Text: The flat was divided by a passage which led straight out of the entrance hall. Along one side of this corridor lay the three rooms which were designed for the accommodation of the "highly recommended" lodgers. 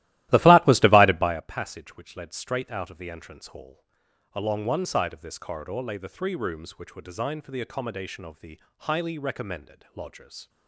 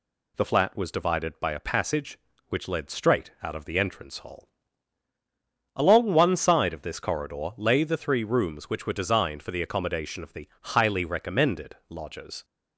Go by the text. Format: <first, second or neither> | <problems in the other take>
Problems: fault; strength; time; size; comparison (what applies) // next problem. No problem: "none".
second | starts louder than the rest; strong; until 1.5 s; 15.5 dB // pauses between "the" and "highly"; slight; at 8.5 s; 0.20 s long